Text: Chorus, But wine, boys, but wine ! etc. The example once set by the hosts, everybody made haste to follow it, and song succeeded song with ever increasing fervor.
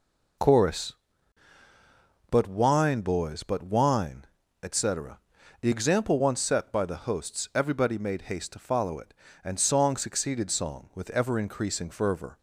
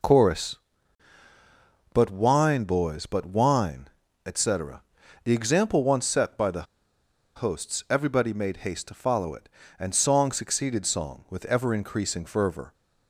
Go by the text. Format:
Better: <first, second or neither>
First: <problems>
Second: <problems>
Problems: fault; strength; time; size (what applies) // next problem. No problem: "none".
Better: first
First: none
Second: pauses between "the" and "hosts"; noticeable; at 6.6 s; 0.72 s long